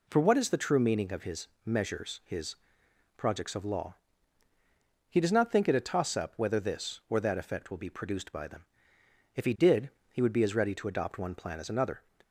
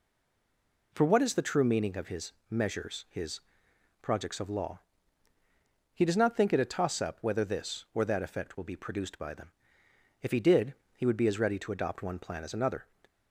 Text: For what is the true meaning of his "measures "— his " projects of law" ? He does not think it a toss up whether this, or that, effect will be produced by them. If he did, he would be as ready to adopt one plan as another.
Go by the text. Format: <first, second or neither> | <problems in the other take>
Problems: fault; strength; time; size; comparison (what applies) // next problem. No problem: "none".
first | stays silent before the first word; slight; until 0.9 s; 0.9 s long // pauses between "his" and "measures"; slight; at 2.3 s; 0.18 s long; slight in the first